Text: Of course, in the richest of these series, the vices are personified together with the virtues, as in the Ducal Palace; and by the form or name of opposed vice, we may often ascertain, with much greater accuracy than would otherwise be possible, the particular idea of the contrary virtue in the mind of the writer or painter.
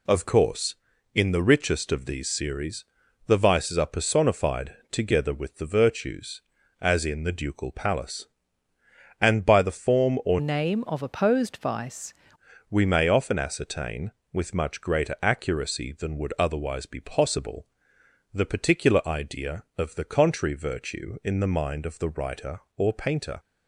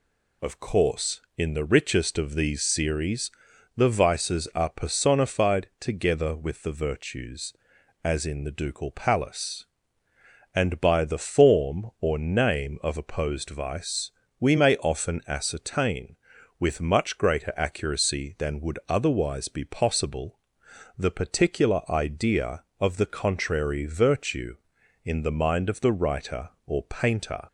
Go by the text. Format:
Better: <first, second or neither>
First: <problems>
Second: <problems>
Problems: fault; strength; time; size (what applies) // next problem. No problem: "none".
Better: second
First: pauses between "personified" and "together"; slight; at 4.7 s; 0.16 s long // changes voice from "name" to "vice"; from 10.3 to 12.1 s; 1.8 s long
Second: none